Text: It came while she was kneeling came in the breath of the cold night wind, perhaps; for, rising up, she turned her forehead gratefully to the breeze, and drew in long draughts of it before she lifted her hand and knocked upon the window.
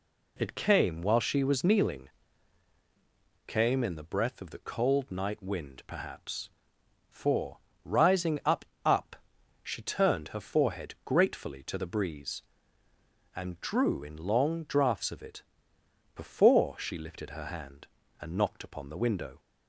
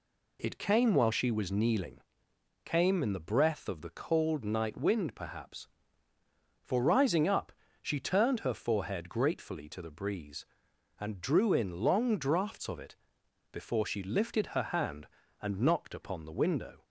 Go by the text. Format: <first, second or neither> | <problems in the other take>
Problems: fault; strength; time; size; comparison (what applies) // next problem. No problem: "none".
second | pauses between "kneeling" and "came"; strong; at 2.0 s; 1.3 s long; noticeable in the second // says "up" twice; at 8.8 s // pauses between "it" and "before"; noticeable; at 15.4 s; 0.70 s long; noticeable in the second